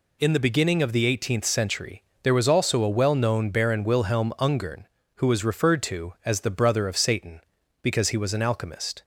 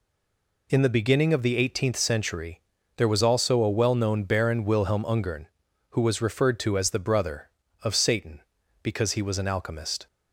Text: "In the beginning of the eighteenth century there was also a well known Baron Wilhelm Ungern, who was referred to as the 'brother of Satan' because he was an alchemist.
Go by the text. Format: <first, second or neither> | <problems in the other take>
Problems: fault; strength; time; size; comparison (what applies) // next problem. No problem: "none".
first | stays silent before the first word; slight; until 0.6 s; 0.6 s long // pauses between "century" and "there"; slight; at 2.6 s; 0.34 s long; slight in the first